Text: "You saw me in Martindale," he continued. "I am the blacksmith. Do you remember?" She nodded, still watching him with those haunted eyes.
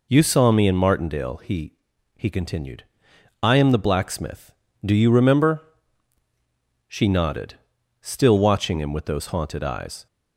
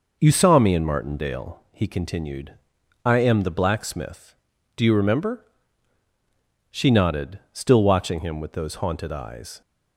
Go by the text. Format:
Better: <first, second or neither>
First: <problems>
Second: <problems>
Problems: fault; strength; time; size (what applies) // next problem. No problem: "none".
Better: second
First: says "he" twice; at 2.1 s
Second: none